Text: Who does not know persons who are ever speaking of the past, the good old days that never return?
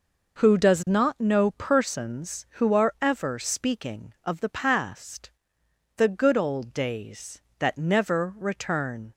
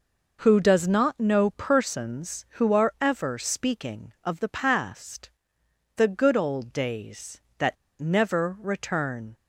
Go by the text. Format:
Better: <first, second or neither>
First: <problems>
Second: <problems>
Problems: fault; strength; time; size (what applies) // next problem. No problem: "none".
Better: first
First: none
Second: pauses between "that" and "never"; slight; at 7.7 s; 0.23 s long